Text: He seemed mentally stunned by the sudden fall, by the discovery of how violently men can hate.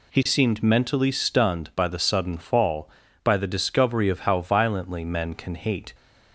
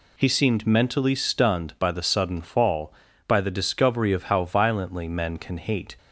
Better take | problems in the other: neither | none

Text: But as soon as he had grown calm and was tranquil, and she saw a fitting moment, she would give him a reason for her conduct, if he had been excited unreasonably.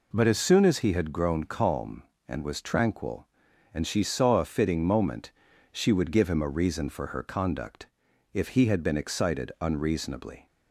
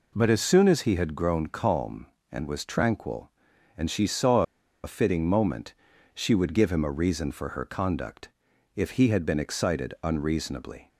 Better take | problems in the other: first | pauses between "saw" and "a"; at 4.4 s; 0.40 s long

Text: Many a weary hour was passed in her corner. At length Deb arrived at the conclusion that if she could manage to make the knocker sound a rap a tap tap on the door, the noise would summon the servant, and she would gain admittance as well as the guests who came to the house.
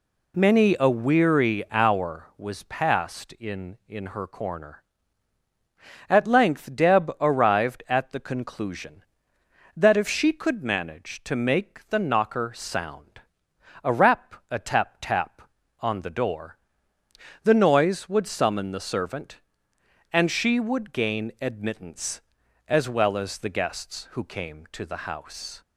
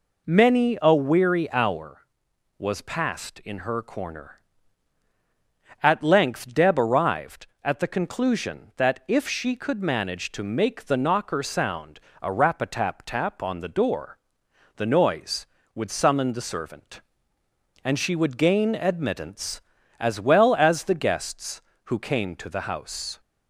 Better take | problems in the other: second | says "in" twice; at 3.8 s // pauses between "sound" and "a"; noticeable; at 13.2 s; 0.60 s long; slight in the second

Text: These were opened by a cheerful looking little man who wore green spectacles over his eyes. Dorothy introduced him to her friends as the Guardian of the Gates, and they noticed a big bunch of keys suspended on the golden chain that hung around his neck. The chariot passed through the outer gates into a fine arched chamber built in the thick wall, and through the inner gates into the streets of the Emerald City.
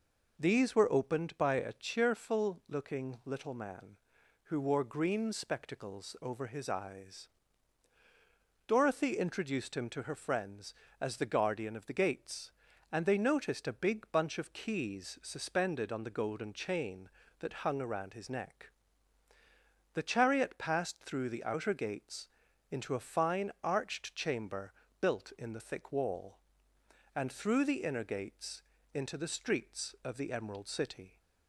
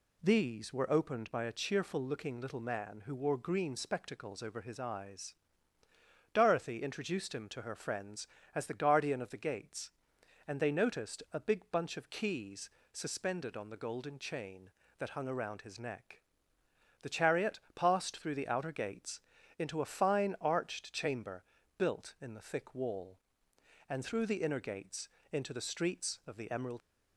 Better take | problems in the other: first | pauses between "keys" and "suspended"; slight; at 12.6 s; 0.22 s long // pauses between "gates" and "into"; slight; at 19.2 s; 0.36 s long; also in the first // pauses between "chamber" and "built"; slight; at 21.4 s; 0.32 s long; slight in the first // pauses between "gates" and "into"; slight; at 25.0 s; 0.24 s long; slight in the first // stops before "City"; at 26.8 s

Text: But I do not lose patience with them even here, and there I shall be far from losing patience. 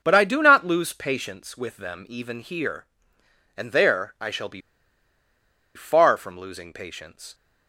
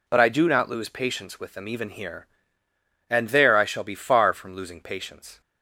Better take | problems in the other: second | pauses between "be" and "far"; at 4.6 s; 1.1 s long

